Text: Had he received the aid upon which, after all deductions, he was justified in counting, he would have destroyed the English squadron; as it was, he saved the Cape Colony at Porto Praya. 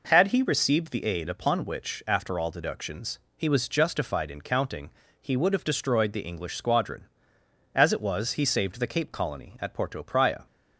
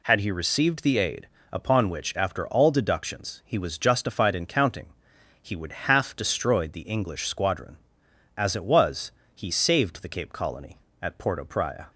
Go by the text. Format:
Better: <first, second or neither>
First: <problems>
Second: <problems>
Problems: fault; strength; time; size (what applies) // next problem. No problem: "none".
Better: first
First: none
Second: pauses between "aid" and "upon"; slight; at 1.2 s; 0.26 s long // says "half" for "have"; at 5.7 s